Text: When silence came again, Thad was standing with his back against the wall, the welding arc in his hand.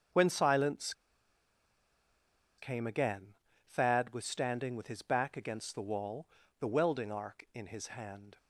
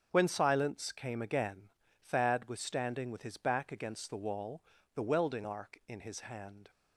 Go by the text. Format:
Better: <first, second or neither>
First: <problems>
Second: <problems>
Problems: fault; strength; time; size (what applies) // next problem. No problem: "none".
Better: second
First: starts louder than the rest; until 2.8 s; 7 dB // pauses between "silence" and "came"; strong; at 0.9 s; 1.6 s long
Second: starts louder than the rest; until 1.1 s; 6.5 dB